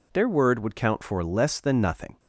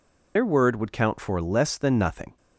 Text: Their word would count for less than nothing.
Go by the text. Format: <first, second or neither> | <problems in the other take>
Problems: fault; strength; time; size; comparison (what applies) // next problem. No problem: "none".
first | loses the start of "Their"; at 0.3 s; 70 ms